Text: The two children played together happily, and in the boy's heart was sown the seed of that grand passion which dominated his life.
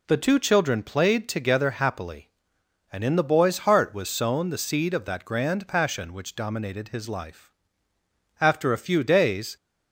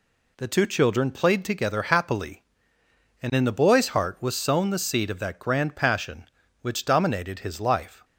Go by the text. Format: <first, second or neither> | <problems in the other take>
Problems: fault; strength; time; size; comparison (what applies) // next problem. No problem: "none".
second | goes on to say "After a few days"; noticeable; from 8.4 s on; 1.1 s long